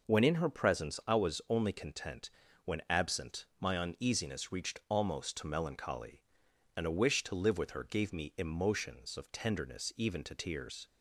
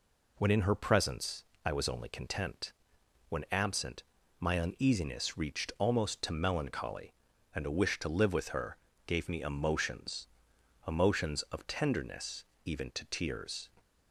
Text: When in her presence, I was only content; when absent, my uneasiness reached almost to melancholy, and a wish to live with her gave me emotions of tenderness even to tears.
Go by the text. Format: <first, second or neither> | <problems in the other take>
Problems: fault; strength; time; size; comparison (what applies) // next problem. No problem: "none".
first | pauses between "her" and "gave"; slight; at 8.7 s; 0.30 s long // says "emotions" twice; at 10.8 s // pauses between "tenderness" and "even"; slight; at 12.4 s; 0.20 s long